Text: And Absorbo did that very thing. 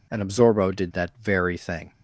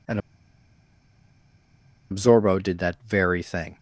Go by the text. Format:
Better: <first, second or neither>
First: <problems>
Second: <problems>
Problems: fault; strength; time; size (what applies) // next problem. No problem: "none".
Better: first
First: none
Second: pauses between "And" and "Absorbo"; strong; at 0.1 s; 1.9 s long